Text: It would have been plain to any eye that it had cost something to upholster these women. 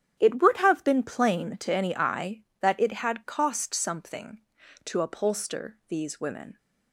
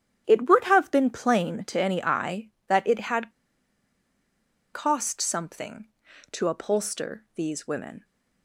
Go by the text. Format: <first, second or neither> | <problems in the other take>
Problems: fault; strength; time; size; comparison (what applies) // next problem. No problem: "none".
first | starts louder than the rest; strong; until 1.2 s; 10 dB; strong in the first // pauses between "had" and "cost"; strong; at 3.2 s; 1.4 s long